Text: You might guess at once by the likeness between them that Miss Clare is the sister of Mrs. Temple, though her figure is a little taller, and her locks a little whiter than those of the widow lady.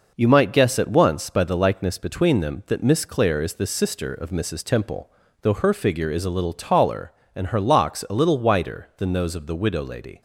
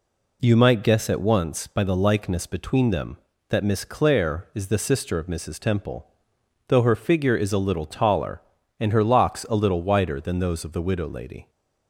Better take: neither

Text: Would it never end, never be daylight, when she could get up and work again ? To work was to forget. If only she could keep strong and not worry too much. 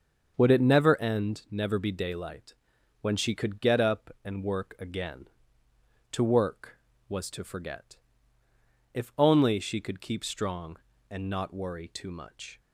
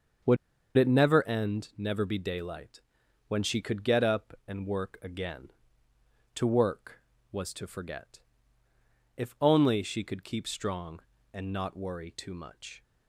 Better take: first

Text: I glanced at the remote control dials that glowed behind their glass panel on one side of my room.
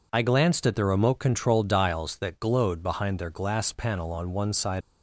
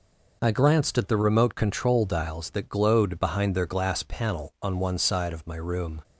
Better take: second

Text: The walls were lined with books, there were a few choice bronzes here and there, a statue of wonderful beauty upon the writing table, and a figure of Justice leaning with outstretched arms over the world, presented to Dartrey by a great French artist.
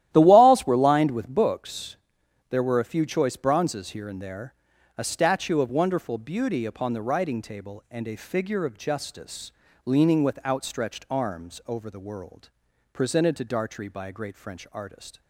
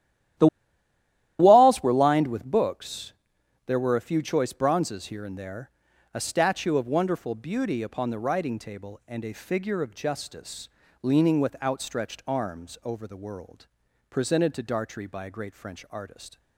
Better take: first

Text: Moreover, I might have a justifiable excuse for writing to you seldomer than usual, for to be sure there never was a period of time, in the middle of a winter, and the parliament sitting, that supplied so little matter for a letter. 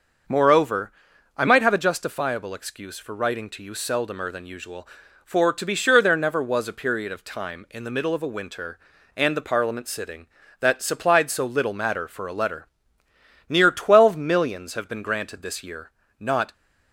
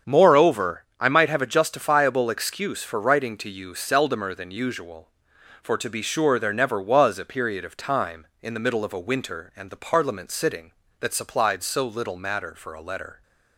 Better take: second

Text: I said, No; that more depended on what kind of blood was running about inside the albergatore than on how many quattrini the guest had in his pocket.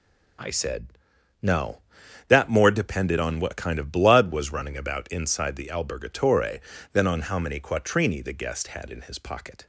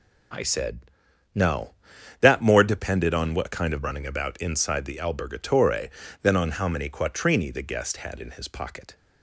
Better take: first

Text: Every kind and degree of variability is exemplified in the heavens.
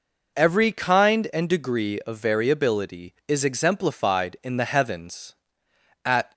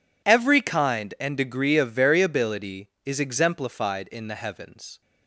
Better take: second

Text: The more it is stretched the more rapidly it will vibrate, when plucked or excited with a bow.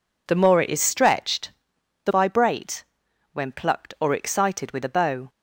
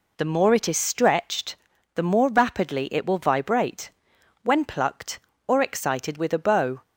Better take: second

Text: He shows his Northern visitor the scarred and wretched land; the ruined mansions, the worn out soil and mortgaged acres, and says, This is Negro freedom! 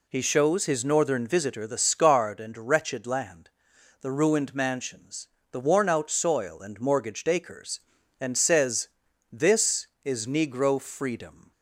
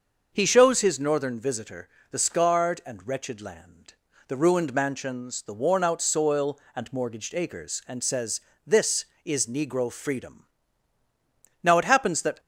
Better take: first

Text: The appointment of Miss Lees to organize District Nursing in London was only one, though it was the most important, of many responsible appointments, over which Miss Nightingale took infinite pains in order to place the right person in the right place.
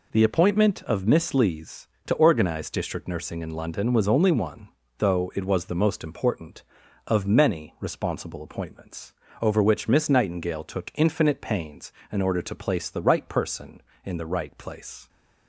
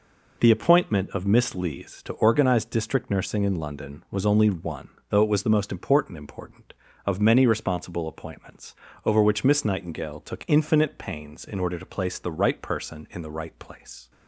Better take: first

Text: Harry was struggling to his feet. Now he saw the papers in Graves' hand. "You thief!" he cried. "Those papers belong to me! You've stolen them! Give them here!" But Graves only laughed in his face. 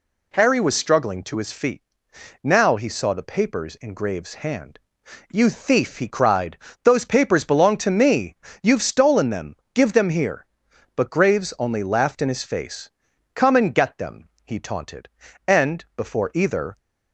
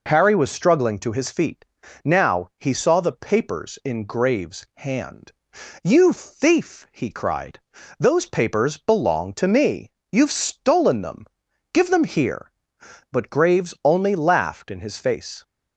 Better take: second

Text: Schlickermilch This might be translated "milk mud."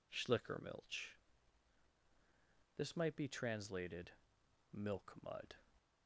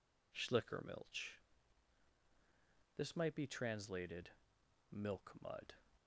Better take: neither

